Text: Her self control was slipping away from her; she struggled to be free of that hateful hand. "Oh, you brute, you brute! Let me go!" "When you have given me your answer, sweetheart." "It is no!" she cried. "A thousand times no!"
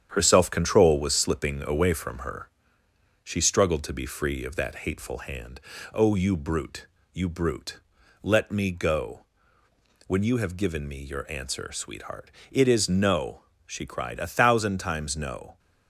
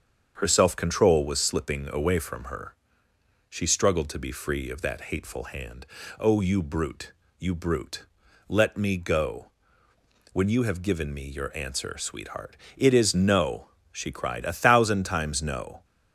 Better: second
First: gets quieter; noticeable; throughout; 5 dB // starts louder than the rest; strong; until 1.1 s; 9 dB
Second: starts louder than the rest; until 1.3 s; 7 dB

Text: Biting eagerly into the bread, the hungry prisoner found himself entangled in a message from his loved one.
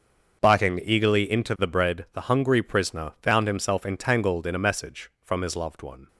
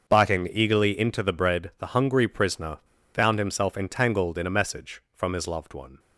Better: first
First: starts louder than the rest; until 1.4 s; 6.5 dB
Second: starts louder than the rest; until 1.1 s; 6.5 dB // pauses between "prisoner" and "found"; slight; at 2.7 s; 0.34 s long

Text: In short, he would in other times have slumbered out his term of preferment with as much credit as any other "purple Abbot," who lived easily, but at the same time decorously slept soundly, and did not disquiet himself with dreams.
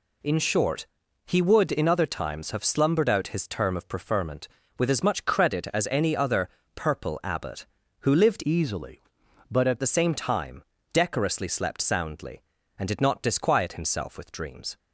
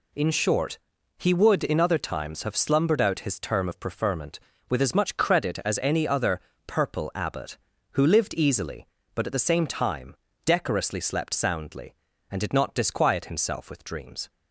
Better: second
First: pauses between "other" and "purple"; slight; at 6.4 s; 0.26 s long // changes voice from "easily" to "at"; from 8.4 to 9.8 s; 1.4 s long // pauses between "time" and "decorously"; slight; at 10.6 s; 0.30 s long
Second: pauses between "other" and "purple"; slight; at 6.4 s; 0.26 s long // pauses between "time" and "decorously"; slight; at 10.1 s; 0.30 s long

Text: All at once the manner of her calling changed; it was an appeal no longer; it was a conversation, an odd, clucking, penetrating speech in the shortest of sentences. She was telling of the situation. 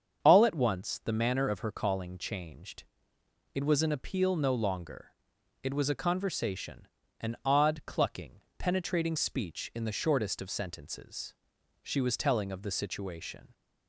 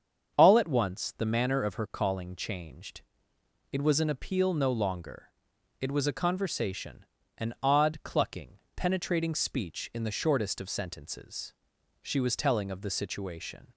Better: neither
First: starts louder than the rest; strong; until 1.2 s; 7.5 dB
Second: starts louder than the rest; strong; until 1.3 s; 7.5 dB

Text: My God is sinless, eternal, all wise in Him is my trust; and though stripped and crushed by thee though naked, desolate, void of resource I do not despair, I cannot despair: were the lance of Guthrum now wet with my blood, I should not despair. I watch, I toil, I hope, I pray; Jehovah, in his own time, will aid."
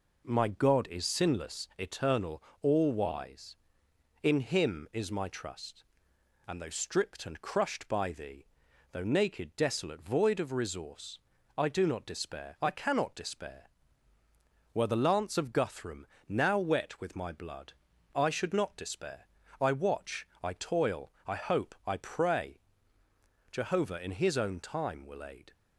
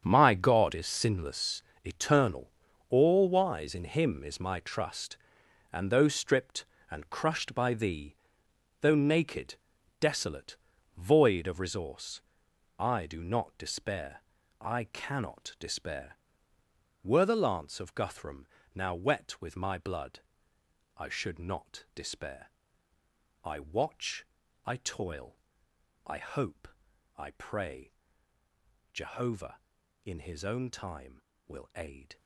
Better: first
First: pauses between "thee" and "though"; noticeable; at 8.4 s; 0.46 s long // pauses between "resource" and "I"; at 11.1 s; 0.40 s long // pauses between "Guthrum" and "now"; slight; at 16.0 s; 0.20 s long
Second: gets quieter; strong; throughout; 13.5 dB // pauses between "thee" and "though"; noticeable; at 8.1 s; 0.68 s long // pauses between "resource" and "I"; noticeable; at 12.1 s; 0.58 s long // pauses between "Guthrum" and "now"; slight; at 18.4 s; 0.28 s long

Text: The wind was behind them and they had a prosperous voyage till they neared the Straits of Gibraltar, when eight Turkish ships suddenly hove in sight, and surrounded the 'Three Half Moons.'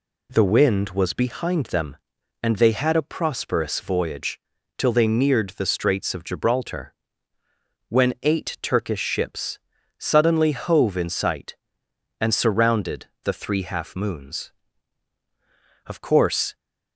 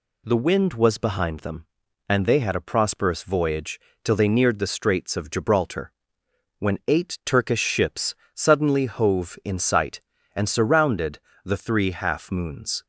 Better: second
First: pauses between "voyage" and "till"; at 4.3 s; 0.40 s long // pauses between "ships" and "suddenly"; at 9.5 s; 0.40 s long // pauses between "surrounded" and "the"; slight; at 13.0 s; 0.18 s long // goes on to say "Of course"; noticeable; from 15.8 s on; 0.70 s long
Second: pauses between "voyage" and "till"; slight; at 3.7 s; 0.24 s long // pauses between "ships" and "suddenly"; slight; at 8.1 s; 0.22 s long // pauses between "surrounded" and "the"; slight; at 11.1 s; 0.28 s long

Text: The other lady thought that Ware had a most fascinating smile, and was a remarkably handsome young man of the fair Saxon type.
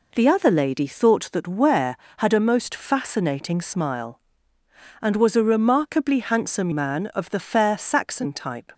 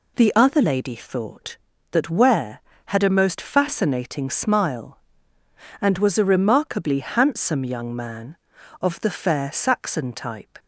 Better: second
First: skips "young"; at 6.7 s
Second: none

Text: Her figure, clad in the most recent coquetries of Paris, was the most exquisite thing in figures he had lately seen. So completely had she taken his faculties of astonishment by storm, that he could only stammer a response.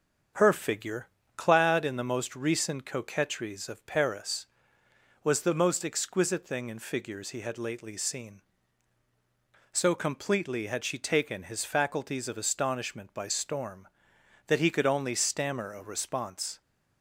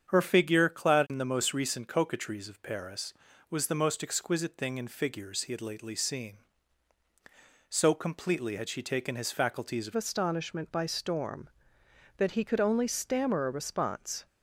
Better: first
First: starts louder than the rest; strong; until 1.6 s; 7 dB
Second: starts louder than the rest; strong; until 1.1 s; 8 dB // changes voice at "astonishment"; from 9.9 s on; 4.3 s long

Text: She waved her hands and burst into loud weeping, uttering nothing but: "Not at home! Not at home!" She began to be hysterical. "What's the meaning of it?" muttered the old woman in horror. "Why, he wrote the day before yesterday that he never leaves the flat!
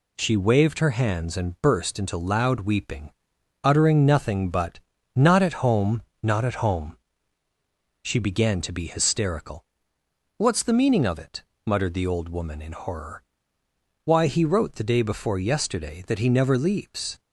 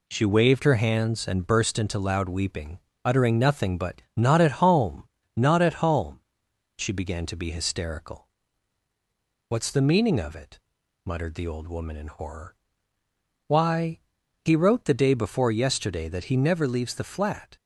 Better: second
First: stops before "the flat"; at 17.1 s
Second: none

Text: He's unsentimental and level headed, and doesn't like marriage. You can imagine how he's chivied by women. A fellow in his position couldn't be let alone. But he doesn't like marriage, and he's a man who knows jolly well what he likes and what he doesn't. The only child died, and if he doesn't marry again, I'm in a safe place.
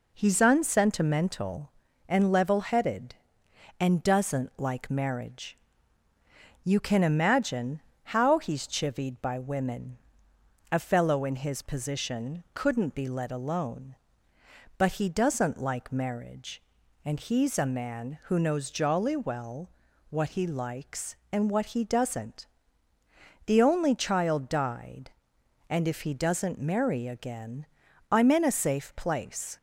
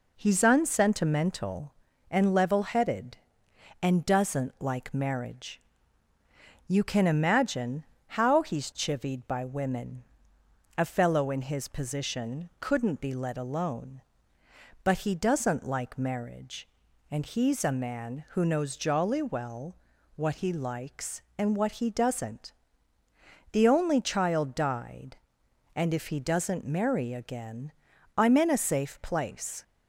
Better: neither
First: pauses between "imagine" and "how"; slight; at 7.8 s; 0.24 s long // pauses between "well" and "what"; at 19.7 s; 0.40 s long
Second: pauses between "imagine" and "how"; slight; at 7.8 s; 0.24 s long // pauses between "well" and "what"; at 19.7 s; 0.40 s long

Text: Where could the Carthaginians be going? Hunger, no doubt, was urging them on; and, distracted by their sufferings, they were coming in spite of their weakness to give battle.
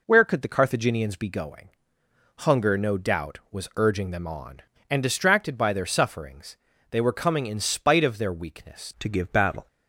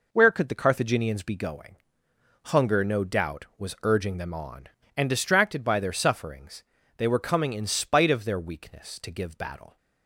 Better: second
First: changes voice at "to"; from 9.0 s on; 0.6 s long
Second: none

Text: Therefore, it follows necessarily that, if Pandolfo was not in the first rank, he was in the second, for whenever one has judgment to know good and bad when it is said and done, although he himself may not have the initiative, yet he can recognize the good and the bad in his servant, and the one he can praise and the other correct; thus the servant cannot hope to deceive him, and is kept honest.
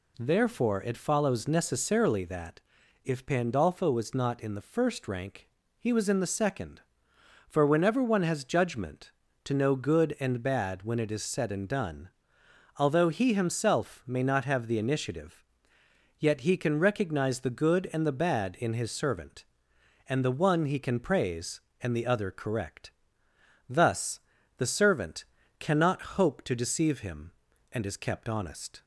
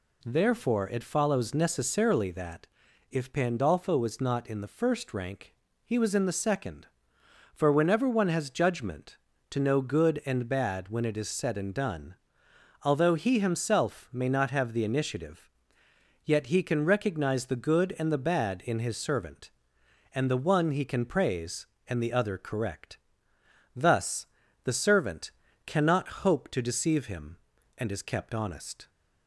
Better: neither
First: pauses between "thus" and "the"; at 24.1 s; 0.38 s long // pauses between "servant" and "cannot"; slight; at 25.2 s; 0.34 s long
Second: pauses between "thus" and "the"; at 24.2 s; 0.38 s long // pauses between "servant" and "cannot"; slight; at 25.3 s; 0.34 s long

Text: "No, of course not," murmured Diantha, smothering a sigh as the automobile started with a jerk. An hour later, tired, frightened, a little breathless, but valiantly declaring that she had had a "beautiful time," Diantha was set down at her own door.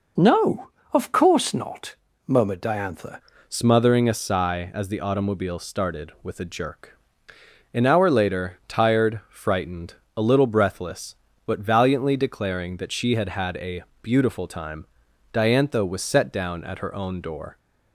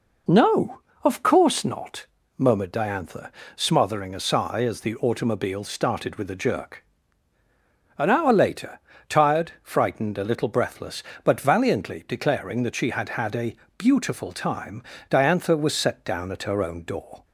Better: second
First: changes voice at "smothering"; from 3.4 s on; 14.1 s long // pauses between "a" and "beautiful"; slight; at 13.8 s; 0.18 s long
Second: pauses between "a" and "beautiful"; slight; at 13.5 s; 0.22 s long

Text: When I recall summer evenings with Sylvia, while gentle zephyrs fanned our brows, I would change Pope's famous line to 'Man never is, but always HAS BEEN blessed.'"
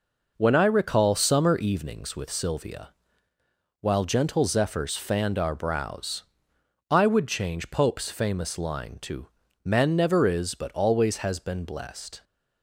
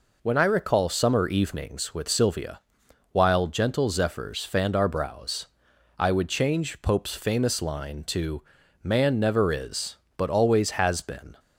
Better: first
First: pauses between "to" and "Man"; at 9.2 s; 0.36 s long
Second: pauses between "to" and "Man"; at 8.4 s; 0.42 s long // stops before "blessed"; at 11.3 s

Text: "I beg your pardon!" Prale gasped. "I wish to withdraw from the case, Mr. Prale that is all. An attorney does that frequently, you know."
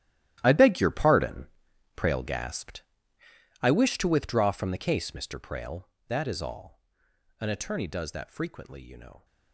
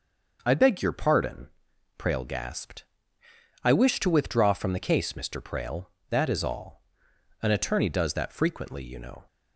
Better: second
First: gets quieter; strong; throughout; 16.5 dB // starts louder than the rest; strong; until 1.4 s; 13 dB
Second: starts louder than the rest; noticeable; until 1.4 s; 6 dB

